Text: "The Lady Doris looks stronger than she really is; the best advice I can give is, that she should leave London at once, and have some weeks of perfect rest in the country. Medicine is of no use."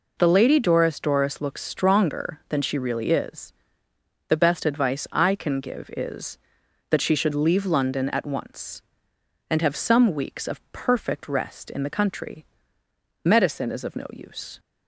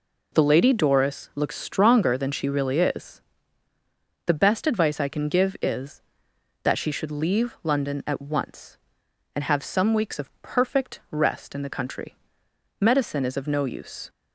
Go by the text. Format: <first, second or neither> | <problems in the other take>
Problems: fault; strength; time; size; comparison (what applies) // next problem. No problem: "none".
second | says "Doris" twice; at 0.9 s